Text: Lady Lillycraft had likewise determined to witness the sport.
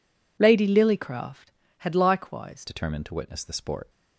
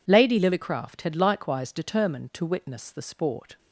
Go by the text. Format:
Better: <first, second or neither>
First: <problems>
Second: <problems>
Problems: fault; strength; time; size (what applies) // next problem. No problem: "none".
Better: second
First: changes voice at "determined"; from 2.6 s on; 1.2 s long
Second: none